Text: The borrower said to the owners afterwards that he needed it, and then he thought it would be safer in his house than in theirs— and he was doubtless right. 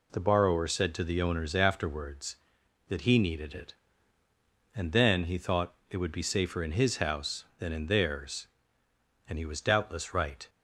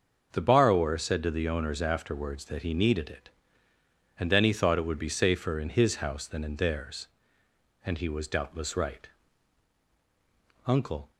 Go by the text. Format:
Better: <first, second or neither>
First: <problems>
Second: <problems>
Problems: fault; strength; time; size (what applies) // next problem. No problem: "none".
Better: first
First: none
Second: starts louder than the rest; until 1.3 s; 6 dB // goes on to say "Uncle"; slight; from 10.6 s on; 0.44 s long